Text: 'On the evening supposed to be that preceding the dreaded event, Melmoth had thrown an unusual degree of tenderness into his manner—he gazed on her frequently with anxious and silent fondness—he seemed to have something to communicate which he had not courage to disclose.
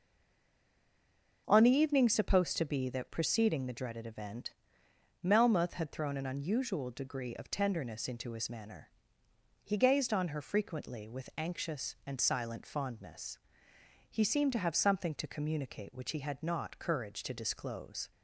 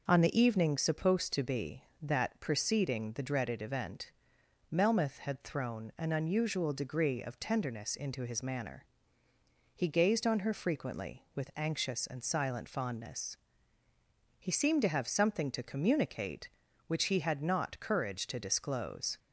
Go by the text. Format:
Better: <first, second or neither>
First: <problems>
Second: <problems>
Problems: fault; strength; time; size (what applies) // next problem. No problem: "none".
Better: second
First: stays silent before the first word; noticeable; until 1.4 s; 1.4 s long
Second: none